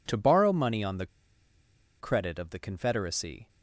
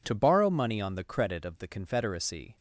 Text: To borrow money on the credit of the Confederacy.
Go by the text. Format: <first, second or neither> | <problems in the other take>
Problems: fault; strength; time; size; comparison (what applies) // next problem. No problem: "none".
second | pauses between "the" and "credit"; noticeable; at 1.0 s; 0.93 s long